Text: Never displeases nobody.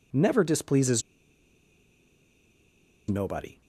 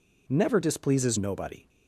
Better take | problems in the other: second | pauses between "displeases" and "nobody"; strong; at 1.0 s; 2.0 s long

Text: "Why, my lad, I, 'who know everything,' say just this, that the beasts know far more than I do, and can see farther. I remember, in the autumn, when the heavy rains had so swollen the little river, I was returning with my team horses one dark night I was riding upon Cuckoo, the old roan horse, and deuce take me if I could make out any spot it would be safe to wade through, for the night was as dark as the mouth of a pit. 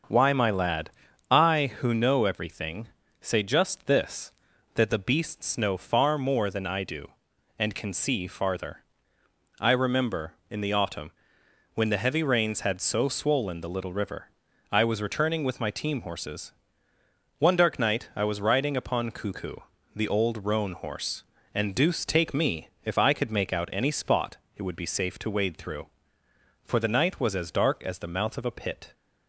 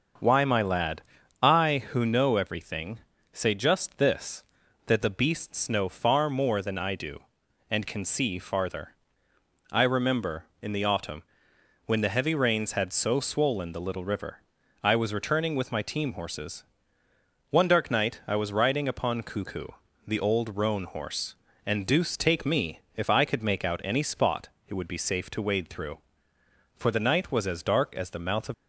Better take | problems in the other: first | starts louder than the rest; until 1.5 s; 6.5 dB; also in the first // pauses between "horses" and "one"; noticeable; at 16.6 s; 0.86 s long; noticeable in the first // pauses between "me" and "if"; slight; at 22.8 s; 0.16 s long; slight in the first // pauses between "spot" and "it"; slight; at 24.4 s; 0.18 s long; slight in the first // stops before "a pit"; at 28.5 s

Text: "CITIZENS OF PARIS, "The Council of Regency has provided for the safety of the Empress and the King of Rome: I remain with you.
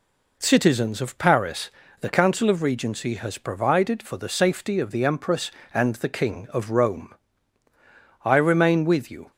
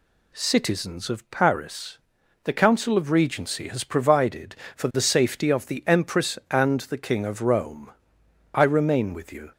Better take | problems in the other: neither | none

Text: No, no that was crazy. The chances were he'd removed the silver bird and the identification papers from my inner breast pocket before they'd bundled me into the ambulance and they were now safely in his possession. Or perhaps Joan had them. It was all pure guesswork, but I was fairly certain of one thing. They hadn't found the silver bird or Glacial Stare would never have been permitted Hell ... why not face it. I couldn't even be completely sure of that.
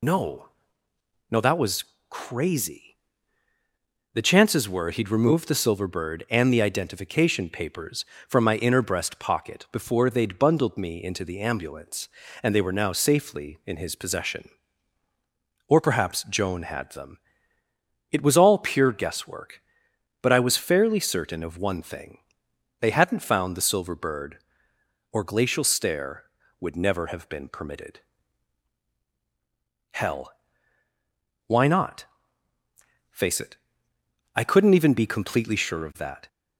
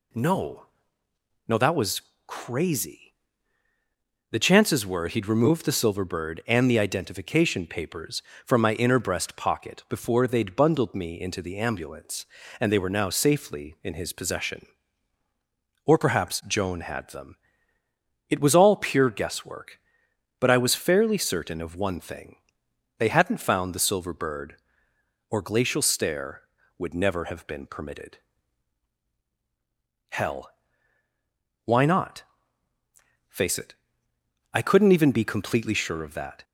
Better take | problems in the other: second | loses the start of "No"; at 0.0 s; 70 ms // pauses between "was" and "crazy"; slight; at 1.8 s; 0.26 s long; slight in the second // pauses between "permitted" and "Hell"; strong; at 27.9 s; 1.9 s long; strong in the second // pauses between "not" and "face"; at 32.0 s; 1.0 s long; also in the second

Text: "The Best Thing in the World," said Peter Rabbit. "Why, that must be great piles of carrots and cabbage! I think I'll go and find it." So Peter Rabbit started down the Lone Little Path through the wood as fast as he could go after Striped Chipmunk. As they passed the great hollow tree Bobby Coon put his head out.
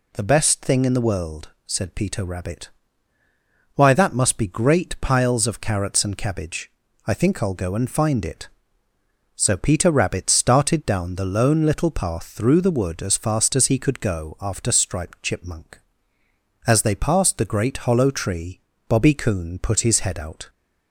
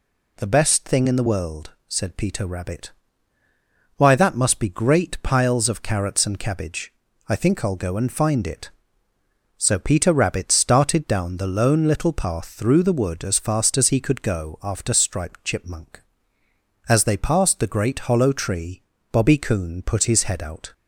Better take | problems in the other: neither | pauses between "tree" and "Bobby"; slight; the same in both

